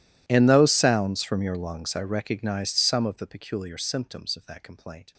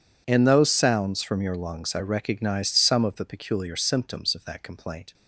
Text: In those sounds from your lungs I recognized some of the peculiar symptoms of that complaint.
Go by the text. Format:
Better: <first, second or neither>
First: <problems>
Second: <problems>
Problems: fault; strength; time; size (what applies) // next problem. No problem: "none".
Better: second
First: gets quieter; strong; throughout; 28.5 dB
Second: none